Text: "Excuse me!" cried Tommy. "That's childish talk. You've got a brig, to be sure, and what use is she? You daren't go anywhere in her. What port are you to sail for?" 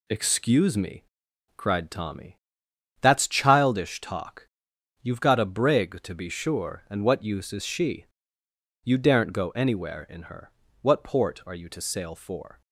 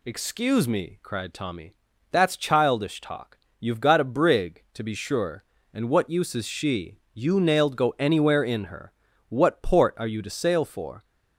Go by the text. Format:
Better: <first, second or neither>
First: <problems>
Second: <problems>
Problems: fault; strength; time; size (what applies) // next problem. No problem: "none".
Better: first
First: none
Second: says "nailed" for "daren't"; at 7.3 s